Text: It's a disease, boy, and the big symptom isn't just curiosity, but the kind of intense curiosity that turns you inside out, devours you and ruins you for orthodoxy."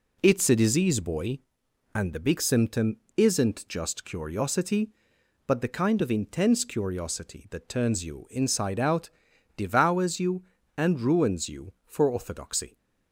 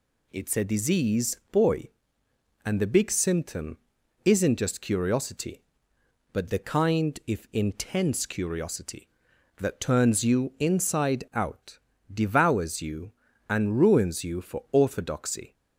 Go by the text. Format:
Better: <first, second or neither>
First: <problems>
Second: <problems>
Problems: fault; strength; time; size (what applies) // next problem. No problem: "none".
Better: first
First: pauses between "symptom" and "isn't"; slight; at 2.9 s; 0.20 s long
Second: pauses between "symptom" and "isn't"; noticeable; at 3.7 s; 0.48 s long // says "if" for "of"; at 7.2 s